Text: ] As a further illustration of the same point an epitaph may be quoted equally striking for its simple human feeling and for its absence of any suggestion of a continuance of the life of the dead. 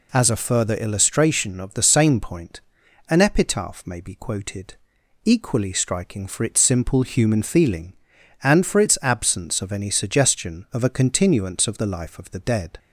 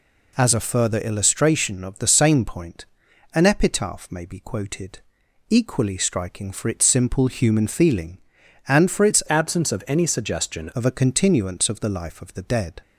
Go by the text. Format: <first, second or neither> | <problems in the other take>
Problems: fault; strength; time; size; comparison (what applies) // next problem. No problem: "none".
first | pauses between "point" and "an"; noticeable; at 2.8 s; 0.50 s long; noticeable in the first // pauses between "quoted" and "equally"; noticeable; at 4.9 s; 0.50 s long; noticeable in the first // changes voice from "absence" to "suggestion"; from 9.2 to 10.7 s; 1.5 s long